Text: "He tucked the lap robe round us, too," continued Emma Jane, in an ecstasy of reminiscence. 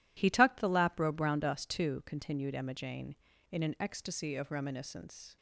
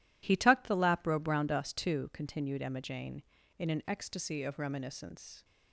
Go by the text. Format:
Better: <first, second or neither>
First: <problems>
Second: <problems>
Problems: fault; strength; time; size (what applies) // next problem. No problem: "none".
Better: neither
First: none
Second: none